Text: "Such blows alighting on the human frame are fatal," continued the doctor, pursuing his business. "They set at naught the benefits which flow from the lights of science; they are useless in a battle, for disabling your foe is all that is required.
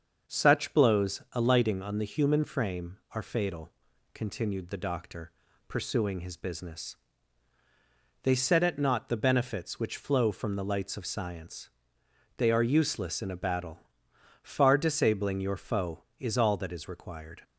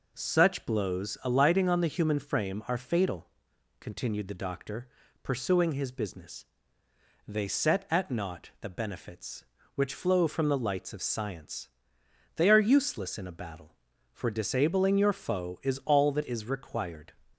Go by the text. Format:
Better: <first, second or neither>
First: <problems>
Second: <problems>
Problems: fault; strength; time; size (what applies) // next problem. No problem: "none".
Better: second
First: starts louder than the rest; until 1.3 s; 6.5 dB // says "far" for "for"; at 14.4 s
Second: none